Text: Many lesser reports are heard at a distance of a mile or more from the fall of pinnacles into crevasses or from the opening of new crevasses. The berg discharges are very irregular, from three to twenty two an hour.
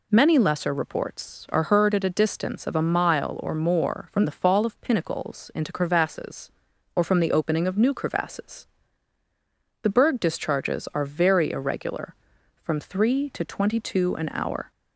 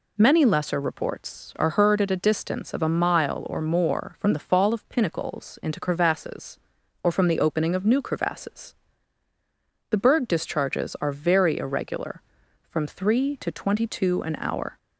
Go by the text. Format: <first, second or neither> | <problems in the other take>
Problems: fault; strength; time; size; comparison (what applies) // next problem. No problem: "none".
neither | none